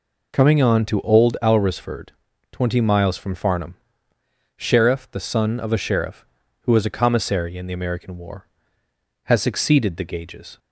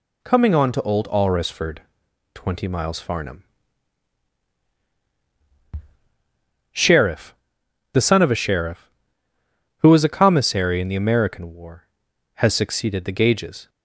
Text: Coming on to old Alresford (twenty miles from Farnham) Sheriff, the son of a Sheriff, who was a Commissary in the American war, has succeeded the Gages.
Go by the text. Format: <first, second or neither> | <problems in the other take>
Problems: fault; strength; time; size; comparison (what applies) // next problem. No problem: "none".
first | skips "from"; at 2.9 s